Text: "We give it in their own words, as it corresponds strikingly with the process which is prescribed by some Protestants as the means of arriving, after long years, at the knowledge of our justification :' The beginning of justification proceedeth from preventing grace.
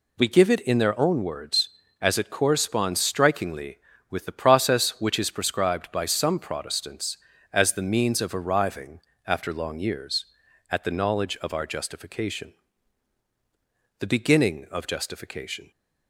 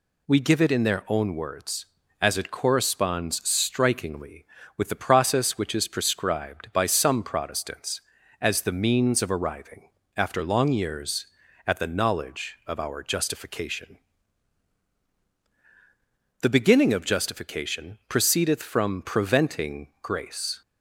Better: second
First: stops before "proceedeth from preventing grace"; at 15.7 s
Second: none

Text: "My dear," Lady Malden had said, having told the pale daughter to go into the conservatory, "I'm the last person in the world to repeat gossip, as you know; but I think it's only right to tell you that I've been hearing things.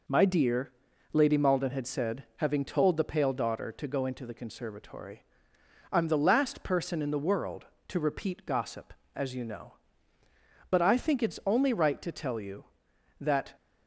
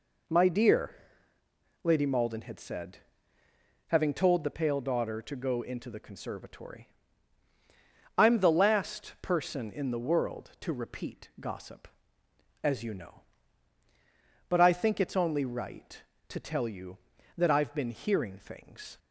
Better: second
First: stops before "I've been hearing things"; at 13.5 s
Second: none

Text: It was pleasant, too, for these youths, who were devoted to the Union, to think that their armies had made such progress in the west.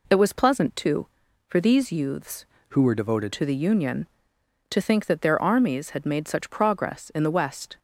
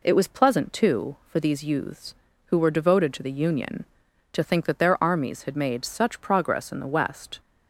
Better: second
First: changes voice from "who" to "devoted"; from 2.6 to 3.3 s; 0.7 s long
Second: none

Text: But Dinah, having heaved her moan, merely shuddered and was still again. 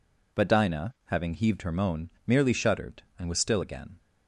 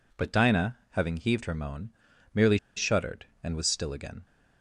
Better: first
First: none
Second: pauses between "merely" and "shuddered"; slight; at 2.5 s; 0.18 s long

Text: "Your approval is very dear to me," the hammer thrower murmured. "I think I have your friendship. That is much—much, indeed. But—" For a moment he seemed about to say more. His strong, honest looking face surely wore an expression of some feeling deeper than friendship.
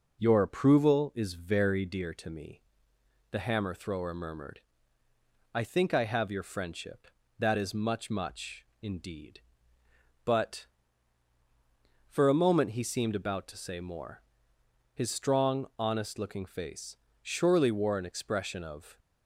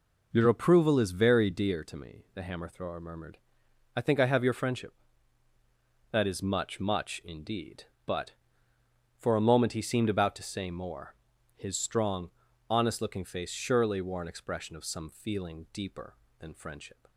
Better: second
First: pauses between "face" and "surely"; slight; at 16.9 s; 0.26 s long // stops before "some feeling deeper than friendship"; at 18.9 s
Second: none

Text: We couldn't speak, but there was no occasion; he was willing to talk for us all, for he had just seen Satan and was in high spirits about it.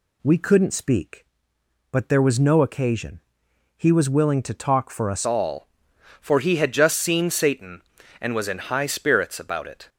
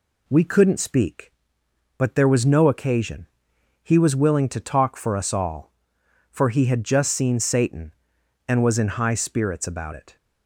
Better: second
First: changes voice at "all"; from 5.2 s on; 4.6 s long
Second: none

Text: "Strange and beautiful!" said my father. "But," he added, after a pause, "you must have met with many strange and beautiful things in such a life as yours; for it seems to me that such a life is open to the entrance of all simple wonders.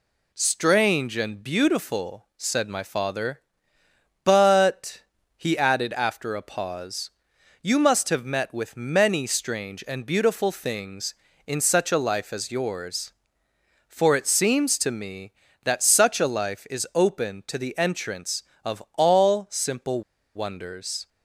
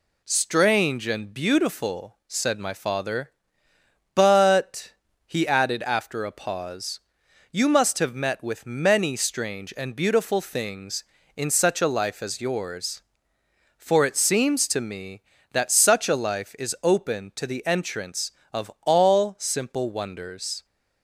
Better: second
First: pauses between "simple" and "wonders"; slight; at 20.0 s; 0.34 s long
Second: none

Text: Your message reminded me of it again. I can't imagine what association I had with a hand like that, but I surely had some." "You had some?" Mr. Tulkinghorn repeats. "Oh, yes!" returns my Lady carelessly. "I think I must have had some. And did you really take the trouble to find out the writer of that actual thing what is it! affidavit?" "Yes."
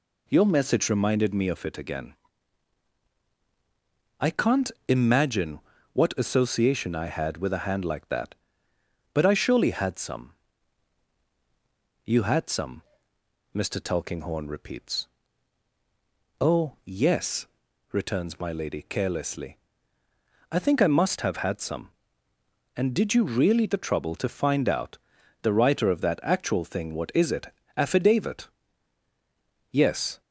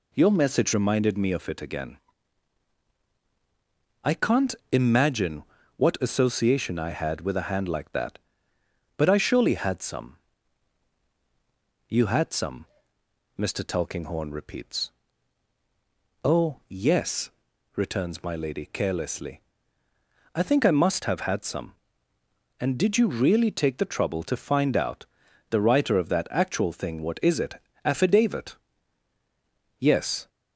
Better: second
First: pauses between "can't" and "imagine"; slight; at 4.7 s; 0.16 s long // pauses between "imagine" and "what"; slight; at 5.6 s; 0.32 s long // skips "take"; at 23.6 s // pauses between "out" and "the"; at 24.9 s; 0.44 s long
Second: pauses between "can't" and "imagine"; slight; at 4.5 s; 0.16 s long // pauses between "imagine" and "what"; slight; at 5.4 s; 0.32 s long // pauses between "out" and "the"; at 25.0 s; 0.44 s long

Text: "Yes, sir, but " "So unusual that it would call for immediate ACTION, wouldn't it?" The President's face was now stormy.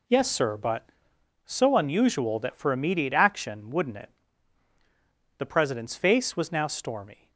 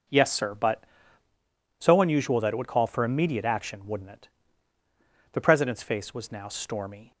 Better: second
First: skips "it would call"; at 2.5 s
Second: none

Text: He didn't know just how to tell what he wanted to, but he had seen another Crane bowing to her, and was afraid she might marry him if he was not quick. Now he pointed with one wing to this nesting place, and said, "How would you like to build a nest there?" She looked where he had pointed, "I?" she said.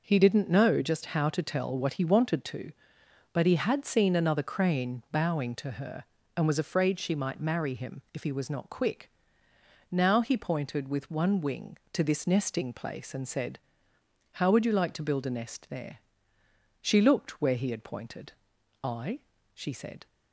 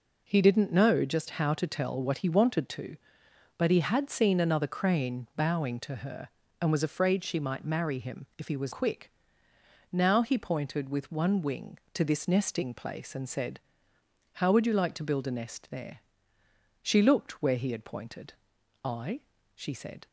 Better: first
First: none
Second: skips "not"; at 8.7 s

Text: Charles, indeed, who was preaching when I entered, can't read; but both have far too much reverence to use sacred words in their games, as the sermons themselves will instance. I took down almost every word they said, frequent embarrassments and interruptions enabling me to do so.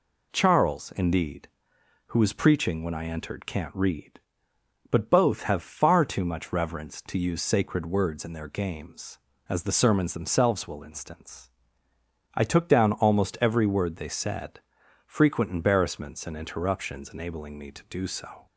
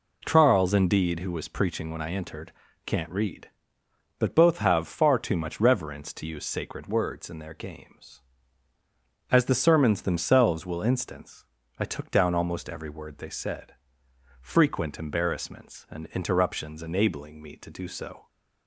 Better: neither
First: none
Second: none

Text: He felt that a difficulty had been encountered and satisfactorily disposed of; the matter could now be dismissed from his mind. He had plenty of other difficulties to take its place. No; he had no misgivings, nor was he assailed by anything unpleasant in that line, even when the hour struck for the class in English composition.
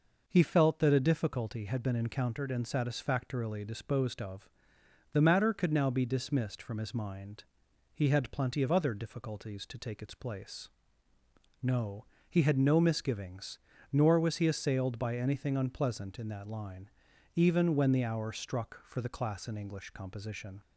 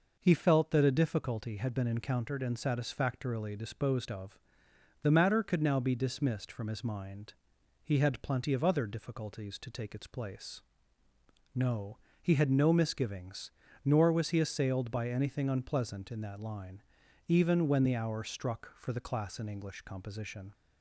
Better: neither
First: none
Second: none

